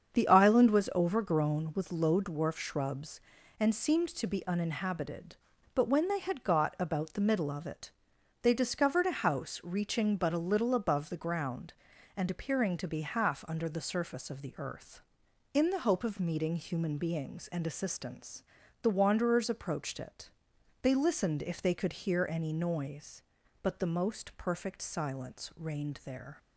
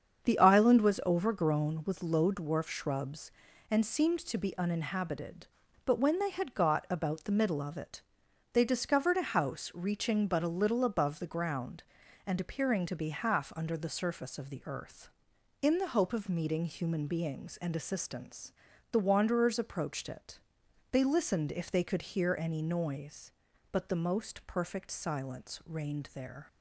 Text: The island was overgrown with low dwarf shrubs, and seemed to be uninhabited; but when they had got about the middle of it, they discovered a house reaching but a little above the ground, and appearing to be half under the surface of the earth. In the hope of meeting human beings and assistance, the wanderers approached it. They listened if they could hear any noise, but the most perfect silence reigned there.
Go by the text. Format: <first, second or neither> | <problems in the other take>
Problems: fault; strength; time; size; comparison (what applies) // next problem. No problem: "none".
neither | starts louder than the rest; strong; the same in both